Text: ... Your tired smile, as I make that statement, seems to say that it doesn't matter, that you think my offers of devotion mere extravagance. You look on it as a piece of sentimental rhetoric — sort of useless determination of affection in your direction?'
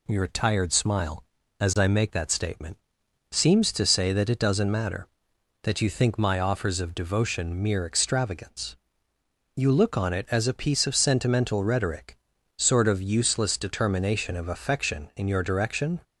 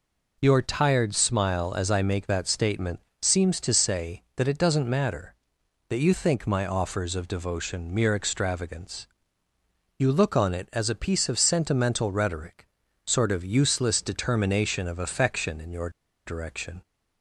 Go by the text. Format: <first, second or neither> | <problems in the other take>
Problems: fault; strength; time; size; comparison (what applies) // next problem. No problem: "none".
first | pauses between "your" and "direction"; at 15.8 s; 0.37 s long